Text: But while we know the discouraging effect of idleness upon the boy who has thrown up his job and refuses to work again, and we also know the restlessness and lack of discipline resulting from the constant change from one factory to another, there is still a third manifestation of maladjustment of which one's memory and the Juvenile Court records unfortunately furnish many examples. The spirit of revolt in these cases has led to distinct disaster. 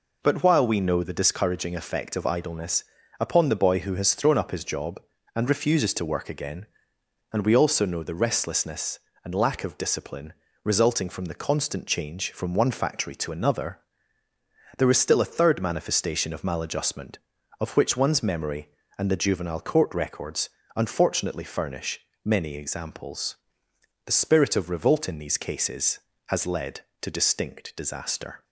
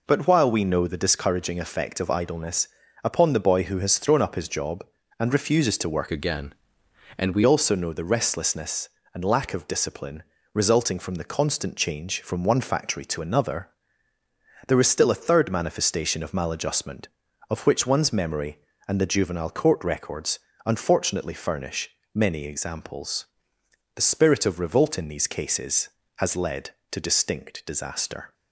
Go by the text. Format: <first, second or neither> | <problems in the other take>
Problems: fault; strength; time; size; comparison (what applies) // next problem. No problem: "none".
first | pauses between "idleness" and "upon"; slight; at 2.6 s; 0.34 s long; slight in the first // changes voice from "again" to "we"; from 6.1 to 7.4 s; 1.3 s long // pauses between "discipline" and "resulting"; slight; at 10.2 s; 0.30 s long; slight in the first // pauses between "records" and "unfortunately"; slight; at 20.3 s; 0.26 s long; slight in the first // pauses between "furnish" and "many"; slight; at 21.8 s; 0.24 s long; slight in the first